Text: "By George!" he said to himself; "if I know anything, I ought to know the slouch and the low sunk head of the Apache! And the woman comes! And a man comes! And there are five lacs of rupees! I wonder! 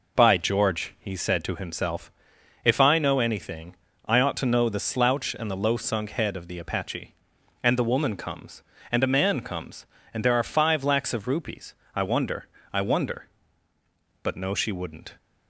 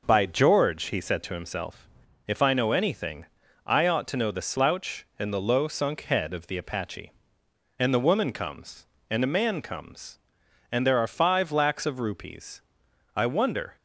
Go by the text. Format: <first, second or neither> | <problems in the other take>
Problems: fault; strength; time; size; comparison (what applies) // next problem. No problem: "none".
second | goes on to say "I wonder But no she wouldn't"; strong; from 12.7 s on; 2.4 s long